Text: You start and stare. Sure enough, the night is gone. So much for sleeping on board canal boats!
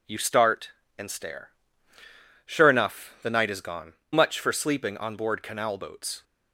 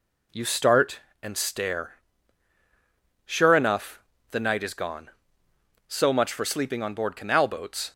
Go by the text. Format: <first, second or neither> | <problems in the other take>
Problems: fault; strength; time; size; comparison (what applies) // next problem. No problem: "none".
second | skips "So"; at 4.0 s